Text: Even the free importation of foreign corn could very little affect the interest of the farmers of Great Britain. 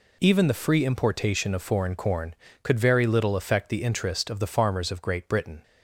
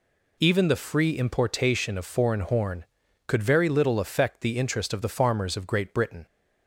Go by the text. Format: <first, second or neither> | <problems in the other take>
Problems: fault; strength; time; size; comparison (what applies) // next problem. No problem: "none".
first | says "horn" for "corn"; at 2.4 s